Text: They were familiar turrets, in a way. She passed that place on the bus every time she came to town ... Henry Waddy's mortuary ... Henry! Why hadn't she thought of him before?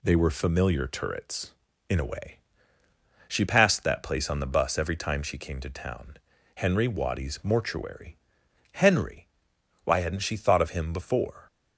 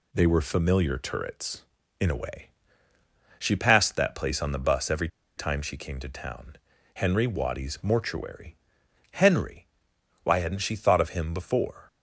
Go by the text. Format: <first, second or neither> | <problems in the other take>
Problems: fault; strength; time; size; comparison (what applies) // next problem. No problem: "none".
first | pauses between "every" and "time"; slight; at 5.0 s; 0.29 s long